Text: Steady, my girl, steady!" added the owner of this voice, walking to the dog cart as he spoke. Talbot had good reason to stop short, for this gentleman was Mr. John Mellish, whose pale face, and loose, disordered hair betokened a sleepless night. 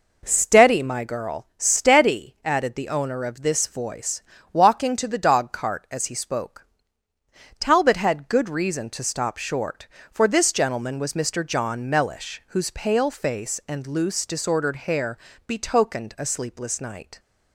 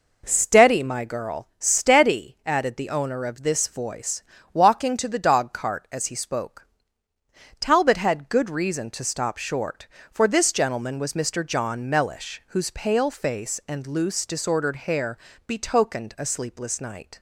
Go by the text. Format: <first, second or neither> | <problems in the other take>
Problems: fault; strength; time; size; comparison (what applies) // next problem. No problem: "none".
neither | pauses between "hair" and "betokened"; slight; the same in both